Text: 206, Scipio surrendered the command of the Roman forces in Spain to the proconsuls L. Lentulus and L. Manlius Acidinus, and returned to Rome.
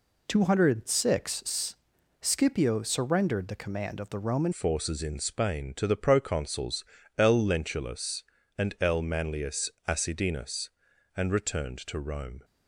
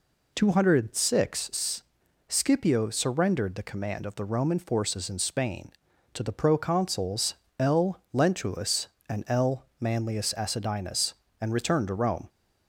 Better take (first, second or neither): second